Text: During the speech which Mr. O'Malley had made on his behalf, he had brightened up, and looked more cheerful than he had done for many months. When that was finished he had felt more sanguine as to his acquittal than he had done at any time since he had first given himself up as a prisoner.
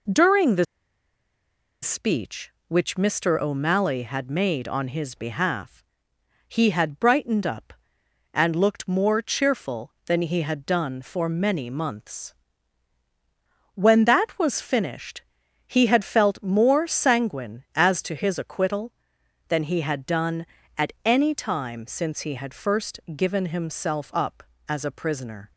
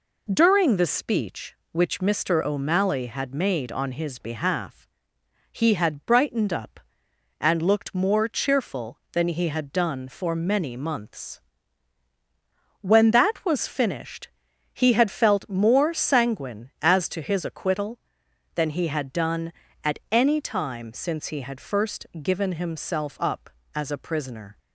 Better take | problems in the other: second | pauses between "the" and "speech"; at 0.6 s; 1.1 s long // pauses between "finished" and "he"; at 15.2 s; 0.44 s long; also in the second // pauses between "first" and "given"; slight; at 22.9 s; 0.16 s long; slight in the second

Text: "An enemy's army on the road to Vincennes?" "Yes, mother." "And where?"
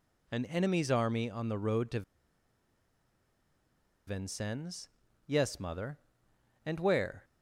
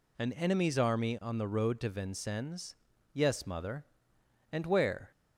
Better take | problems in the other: second | pauses between "to" and "Vincennes"; strong; at 2.0 s; 2.0 s long

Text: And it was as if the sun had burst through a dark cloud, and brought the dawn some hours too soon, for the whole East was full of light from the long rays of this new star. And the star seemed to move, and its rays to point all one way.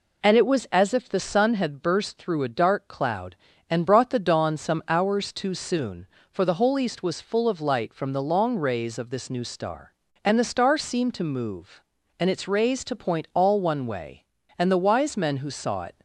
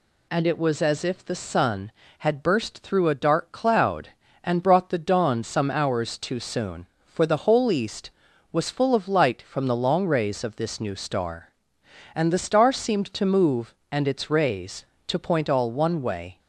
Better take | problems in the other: second | goes on to say "And the wise men who saw it"; from 14.5 s on; 1.3 s long

